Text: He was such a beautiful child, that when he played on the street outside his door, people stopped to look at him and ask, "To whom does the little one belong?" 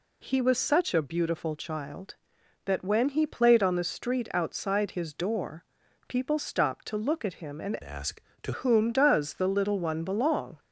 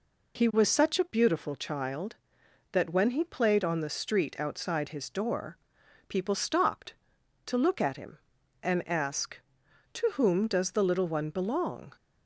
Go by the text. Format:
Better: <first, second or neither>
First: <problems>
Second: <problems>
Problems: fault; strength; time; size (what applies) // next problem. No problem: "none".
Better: second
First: changes voice from "ask" to "To"; from 7.8 to 8.5 s; 0.7 s long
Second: none